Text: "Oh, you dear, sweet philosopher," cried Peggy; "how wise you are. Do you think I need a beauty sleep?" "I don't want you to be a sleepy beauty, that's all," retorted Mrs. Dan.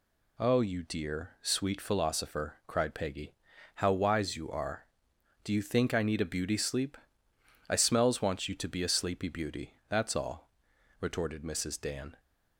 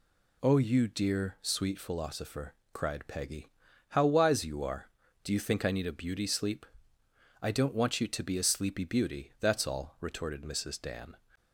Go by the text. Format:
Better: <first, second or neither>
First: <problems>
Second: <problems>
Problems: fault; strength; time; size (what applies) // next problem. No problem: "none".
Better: second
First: says "smells" for "don't"; at 7.7 s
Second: none